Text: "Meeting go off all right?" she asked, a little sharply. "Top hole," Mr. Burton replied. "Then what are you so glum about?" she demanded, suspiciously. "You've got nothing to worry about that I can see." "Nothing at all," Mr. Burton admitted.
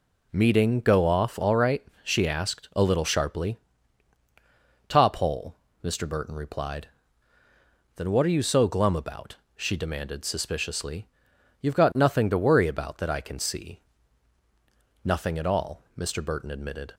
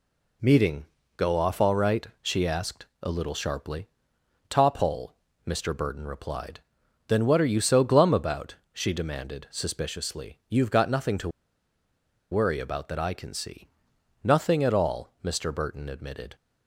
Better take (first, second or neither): first